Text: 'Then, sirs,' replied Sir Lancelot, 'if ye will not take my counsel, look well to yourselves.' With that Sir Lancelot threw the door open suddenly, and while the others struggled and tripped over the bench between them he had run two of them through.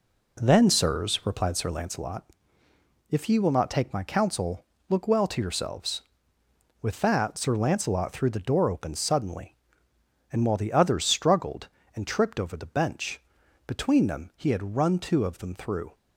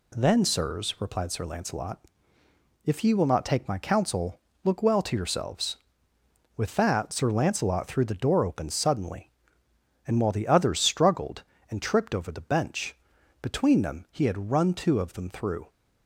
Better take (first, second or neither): second